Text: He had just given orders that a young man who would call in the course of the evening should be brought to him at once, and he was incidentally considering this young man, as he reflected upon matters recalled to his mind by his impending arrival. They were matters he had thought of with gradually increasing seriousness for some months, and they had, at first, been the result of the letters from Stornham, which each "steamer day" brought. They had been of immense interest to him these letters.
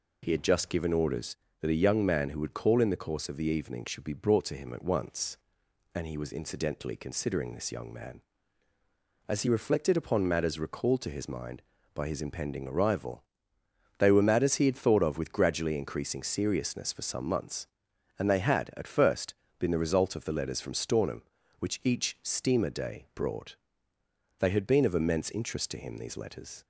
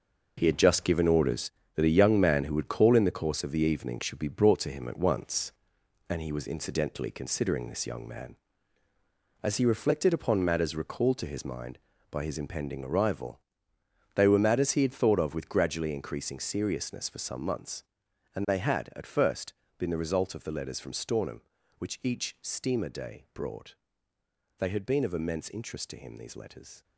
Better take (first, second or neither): first